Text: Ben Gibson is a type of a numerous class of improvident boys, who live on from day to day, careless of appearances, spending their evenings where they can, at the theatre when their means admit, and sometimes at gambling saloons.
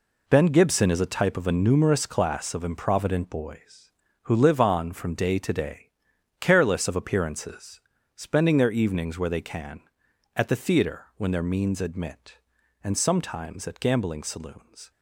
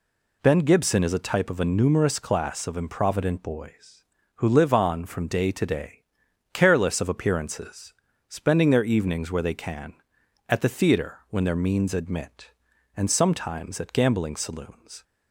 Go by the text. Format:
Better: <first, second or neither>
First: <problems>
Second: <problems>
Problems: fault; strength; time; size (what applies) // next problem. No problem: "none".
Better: second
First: gets quieter; strong; throughout; 9.5 dB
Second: none